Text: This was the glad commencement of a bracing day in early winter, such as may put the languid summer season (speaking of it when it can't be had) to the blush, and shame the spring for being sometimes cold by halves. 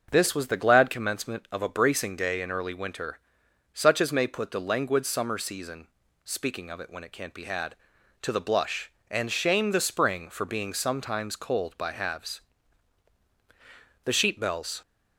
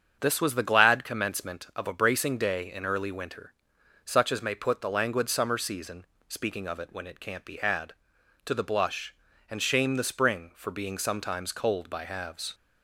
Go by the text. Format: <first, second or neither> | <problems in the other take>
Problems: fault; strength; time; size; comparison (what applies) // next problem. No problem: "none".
second | starts louder than the rest; until 1.1 s; 6.5 dB; strong in the second // goes on to say "The sheep bells"; noticeable; from 14.0 s on; 0.76 s long